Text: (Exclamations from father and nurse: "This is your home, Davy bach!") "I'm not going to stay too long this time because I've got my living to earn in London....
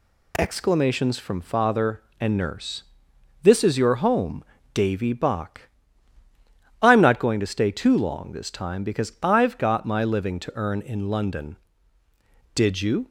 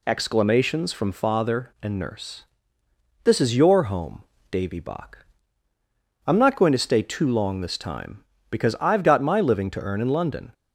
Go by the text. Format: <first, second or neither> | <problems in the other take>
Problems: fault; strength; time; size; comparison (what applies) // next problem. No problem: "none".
second | goes on to say "Did you"; from 12.5 s on; 0.54 s long